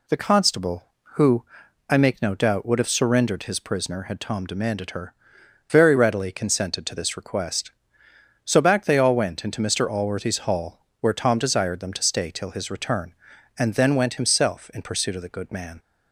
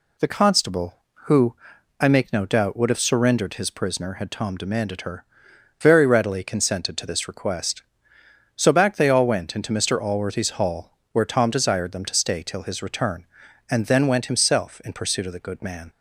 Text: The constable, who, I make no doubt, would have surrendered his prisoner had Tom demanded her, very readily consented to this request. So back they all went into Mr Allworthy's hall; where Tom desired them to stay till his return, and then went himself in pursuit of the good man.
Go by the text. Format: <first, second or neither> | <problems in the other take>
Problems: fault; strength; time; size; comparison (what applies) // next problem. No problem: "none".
neither | none